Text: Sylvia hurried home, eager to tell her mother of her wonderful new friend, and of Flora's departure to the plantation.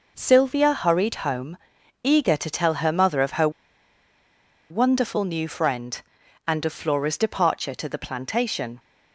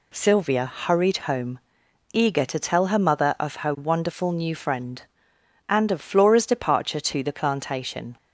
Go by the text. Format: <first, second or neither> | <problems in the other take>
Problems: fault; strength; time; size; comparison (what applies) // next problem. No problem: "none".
second | pauses between "her" and "wonderful"; at 3.4 s; 1.2 s long